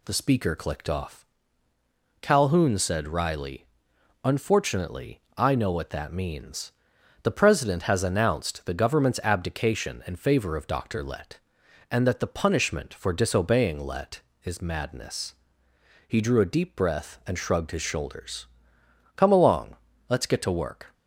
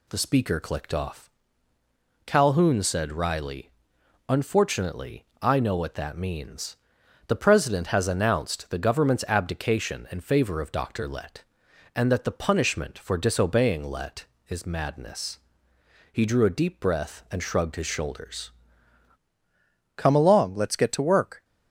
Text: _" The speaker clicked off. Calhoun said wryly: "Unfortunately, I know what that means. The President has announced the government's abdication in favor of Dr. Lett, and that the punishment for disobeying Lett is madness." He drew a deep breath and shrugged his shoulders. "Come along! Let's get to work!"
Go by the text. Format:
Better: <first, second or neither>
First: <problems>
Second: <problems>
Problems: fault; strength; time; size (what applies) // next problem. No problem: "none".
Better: first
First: none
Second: changes voice at "Come"; from 19.9 s on; 1.5 s long